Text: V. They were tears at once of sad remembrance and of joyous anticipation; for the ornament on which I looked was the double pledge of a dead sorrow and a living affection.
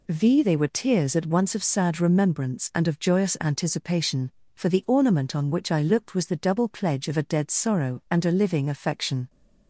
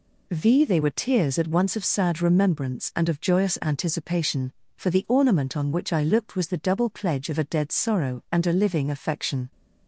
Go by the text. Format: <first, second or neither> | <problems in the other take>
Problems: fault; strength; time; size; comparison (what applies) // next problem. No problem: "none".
neither | none